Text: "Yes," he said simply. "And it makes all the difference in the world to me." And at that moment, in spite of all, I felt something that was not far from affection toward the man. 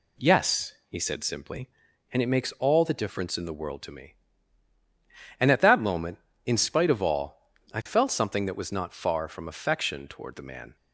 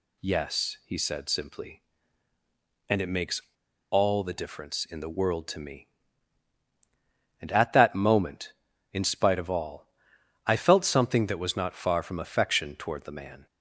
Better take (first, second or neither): first